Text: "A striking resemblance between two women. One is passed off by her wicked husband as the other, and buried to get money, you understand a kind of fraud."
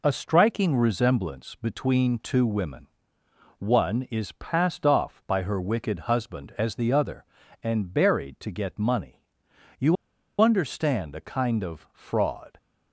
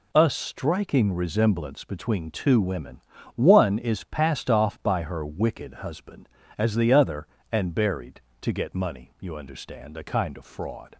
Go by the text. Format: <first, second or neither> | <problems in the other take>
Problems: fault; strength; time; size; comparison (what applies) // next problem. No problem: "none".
second | pauses between "you" and "understand"; at 9.9 s; 0.45 s long